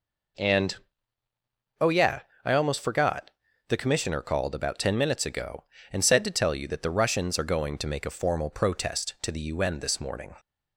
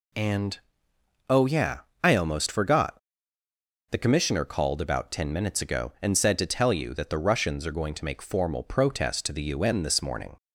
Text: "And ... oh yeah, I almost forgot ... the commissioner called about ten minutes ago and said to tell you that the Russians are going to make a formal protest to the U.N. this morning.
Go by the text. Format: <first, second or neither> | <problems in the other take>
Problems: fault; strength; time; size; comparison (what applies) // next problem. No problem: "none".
first | skips "a"; at 8.2 s